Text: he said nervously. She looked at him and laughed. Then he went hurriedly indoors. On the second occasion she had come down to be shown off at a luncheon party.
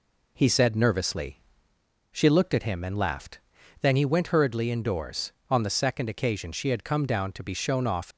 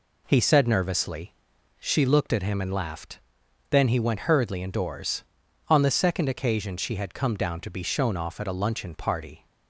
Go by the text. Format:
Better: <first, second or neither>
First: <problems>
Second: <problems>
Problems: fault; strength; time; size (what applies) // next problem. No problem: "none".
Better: second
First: stops before "at a luncheon party"; at 8.1 s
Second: none